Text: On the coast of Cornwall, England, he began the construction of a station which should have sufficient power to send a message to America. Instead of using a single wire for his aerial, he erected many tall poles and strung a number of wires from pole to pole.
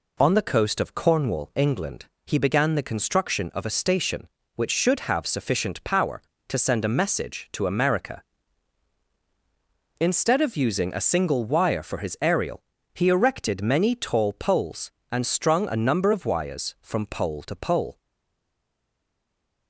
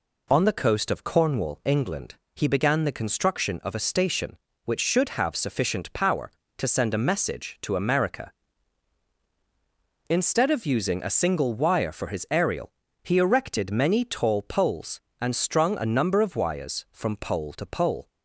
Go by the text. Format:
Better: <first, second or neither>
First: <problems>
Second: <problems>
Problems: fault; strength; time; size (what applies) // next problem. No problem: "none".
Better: second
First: stays silent after the last word; noticeable; from 17.9 s on; 1.7 s long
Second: none